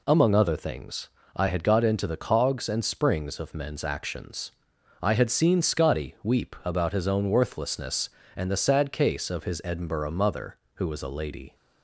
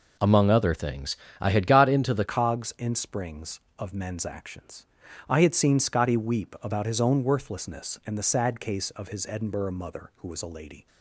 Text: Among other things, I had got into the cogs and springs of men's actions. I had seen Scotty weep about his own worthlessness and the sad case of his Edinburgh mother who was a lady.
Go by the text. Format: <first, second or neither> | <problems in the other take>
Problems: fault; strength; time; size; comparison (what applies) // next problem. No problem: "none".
first | changes voice at "cogs"; from 2.2 s on; 8.6 s long